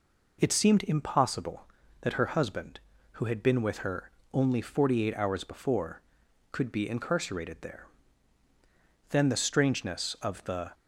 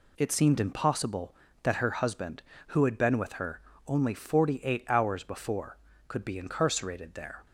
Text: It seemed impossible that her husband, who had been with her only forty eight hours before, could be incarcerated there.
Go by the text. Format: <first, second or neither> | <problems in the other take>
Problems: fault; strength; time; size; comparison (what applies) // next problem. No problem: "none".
second | pauses between "her" and "only"; slight; at 4.0 s; 0.22 s long; slight in the second // goes on to say "Then the strangeness of the"; from 9.0 s on; 1.6 s long